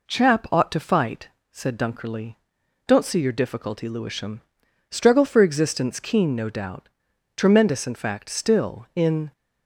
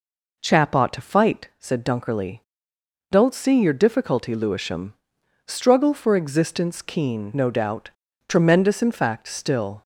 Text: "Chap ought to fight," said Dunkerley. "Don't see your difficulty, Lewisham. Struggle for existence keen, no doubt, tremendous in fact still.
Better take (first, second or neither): second